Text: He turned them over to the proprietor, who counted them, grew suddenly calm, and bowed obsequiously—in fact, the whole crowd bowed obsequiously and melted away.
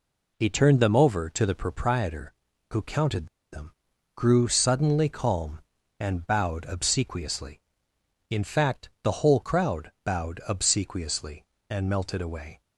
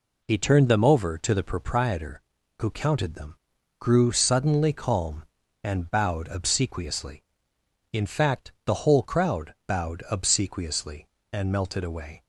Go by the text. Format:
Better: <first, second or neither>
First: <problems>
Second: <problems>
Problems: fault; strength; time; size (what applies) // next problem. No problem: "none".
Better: second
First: pauses between "counted" and "them"; slight; at 3.2 s; 0.25 s long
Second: none